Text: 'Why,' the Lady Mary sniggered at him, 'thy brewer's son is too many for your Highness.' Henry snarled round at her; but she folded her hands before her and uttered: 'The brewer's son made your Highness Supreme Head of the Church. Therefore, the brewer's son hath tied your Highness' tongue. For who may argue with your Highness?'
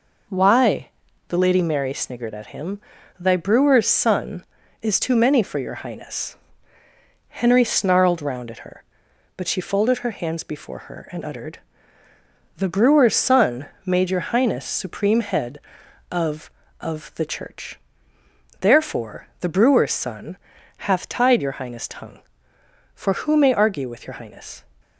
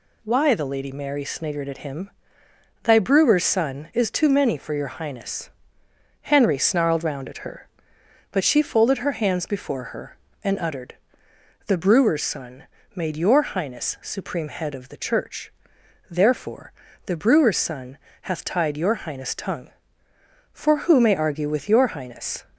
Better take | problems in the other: second | pauses between "son" and "made"; slight; at 13.6 s; 0.18 s long; slight in the second // says "of" twice; at 16.8 s // pauses between "son" and "hath"; noticeable; at 20.3 s; 0.48 s long; slight in the second

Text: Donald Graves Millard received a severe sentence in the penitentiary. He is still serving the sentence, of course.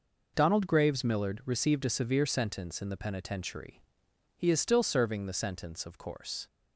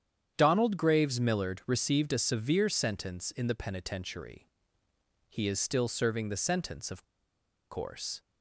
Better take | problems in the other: first | starts louder than the rest; strong; until 1.3 s; 9 dB // pauses between "of" and "course"; noticeable; at 7.0 s; 0.66 s long

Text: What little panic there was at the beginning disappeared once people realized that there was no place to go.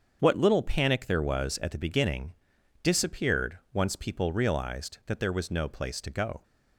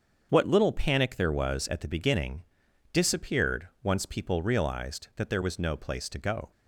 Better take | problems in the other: neither | starts louder than the rest; strong; the same in both // pauses between "beginning" and "disappeared"; noticeable; the same in both

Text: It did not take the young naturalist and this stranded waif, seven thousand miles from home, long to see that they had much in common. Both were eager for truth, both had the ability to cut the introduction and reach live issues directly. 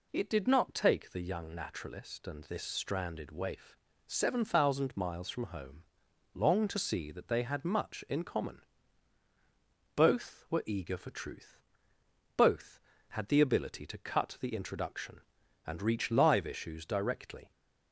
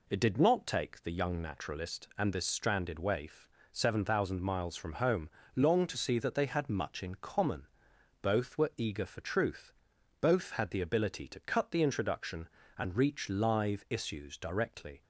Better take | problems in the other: neither | none

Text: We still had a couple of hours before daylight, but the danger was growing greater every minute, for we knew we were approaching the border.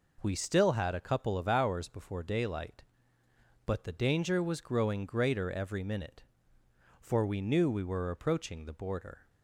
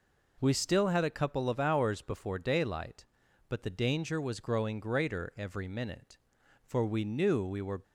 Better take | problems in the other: first | stops before "approaching the border"; at 7.8 s

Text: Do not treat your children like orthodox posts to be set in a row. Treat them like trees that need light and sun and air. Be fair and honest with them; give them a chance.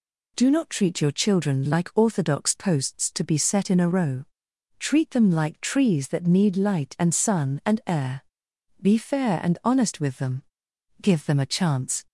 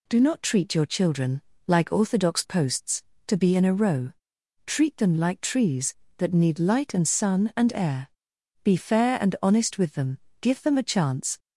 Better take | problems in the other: first | pauses between "children" and "like"; slight; at 1.4 s; 0.24 s long // skips "set"; at 3.5 s

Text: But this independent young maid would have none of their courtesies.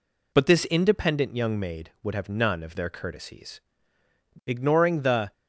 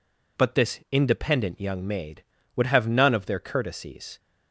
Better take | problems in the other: second | goes on to say "Ignoring the"; noticeable; from 4.4 s on; 0.86 s long

